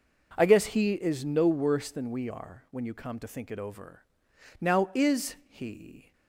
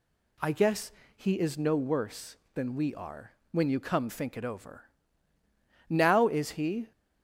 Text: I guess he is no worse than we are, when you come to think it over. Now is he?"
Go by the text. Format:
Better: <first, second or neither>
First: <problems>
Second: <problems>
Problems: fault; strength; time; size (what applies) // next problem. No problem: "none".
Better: first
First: none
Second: pauses between "guess" and "he"; slight; at 0.9 s; 0.24 s long // skips "to"; at 4.0 s